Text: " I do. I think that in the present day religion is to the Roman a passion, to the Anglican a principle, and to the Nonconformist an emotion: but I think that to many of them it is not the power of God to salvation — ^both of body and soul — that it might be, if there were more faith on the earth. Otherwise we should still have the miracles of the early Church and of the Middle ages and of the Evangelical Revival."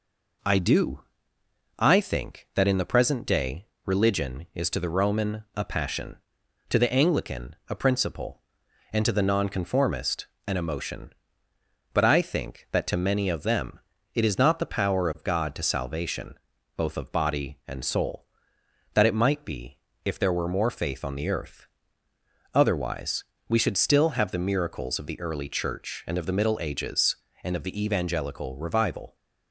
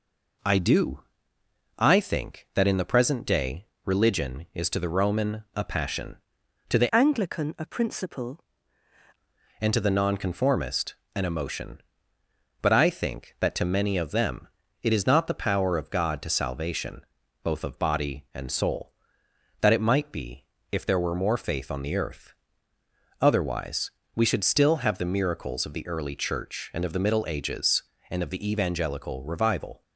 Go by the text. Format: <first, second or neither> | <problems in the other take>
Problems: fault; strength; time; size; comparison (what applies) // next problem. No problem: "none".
first | pauses between "day" and "religion"; slight; at 3.6 s; 0.18 s long; slight in the first // changes voice from "Anglican" to "principle"; from 6.9 to 8.4 s; 1.5 s long // pauses between "Nonconformist" and "an"; slight; at 10.9 s; 0.18 s long; slight in the first // pauses between "them" and "it"; slight; at 14.4 s; 0.34 s long; slight in the first // pauses between "Otherwise" and "we"; slight; at 23.9 s; 0.24 s long; slight in the first